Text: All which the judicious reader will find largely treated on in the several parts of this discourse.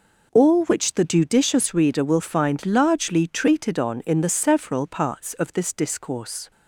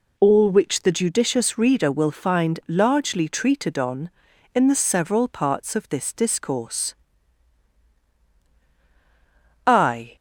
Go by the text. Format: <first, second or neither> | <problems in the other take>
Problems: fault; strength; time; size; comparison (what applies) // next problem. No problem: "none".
first | goes on to say "I"; slight; from 9.6 s on; 0.48 s long